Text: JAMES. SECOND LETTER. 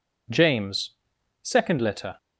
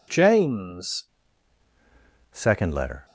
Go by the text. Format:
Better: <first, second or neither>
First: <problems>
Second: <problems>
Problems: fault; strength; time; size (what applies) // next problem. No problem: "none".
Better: first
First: none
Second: changes voice at "SECOND"; from 2.3 s on; 0.7 s long